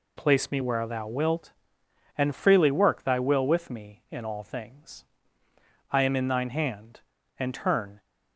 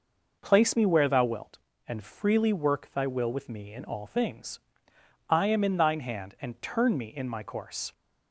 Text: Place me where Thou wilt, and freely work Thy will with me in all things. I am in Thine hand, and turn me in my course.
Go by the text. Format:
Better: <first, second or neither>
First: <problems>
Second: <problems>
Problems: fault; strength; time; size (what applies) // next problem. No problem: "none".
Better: second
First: stops before "me in my course"; at 7.9 s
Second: none